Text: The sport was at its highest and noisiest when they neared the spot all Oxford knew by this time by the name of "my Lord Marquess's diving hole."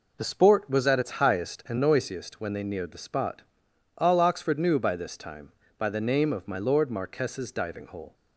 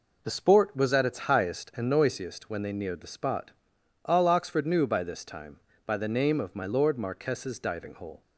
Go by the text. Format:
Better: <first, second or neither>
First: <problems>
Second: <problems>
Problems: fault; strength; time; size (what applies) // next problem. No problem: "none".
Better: neither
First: pauses between "spot" and "all"; noticeable; at 3.4 s; 0.54 s long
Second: pauses between "spot" and "all"; noticeable; at 3.5 s; 0.52 s long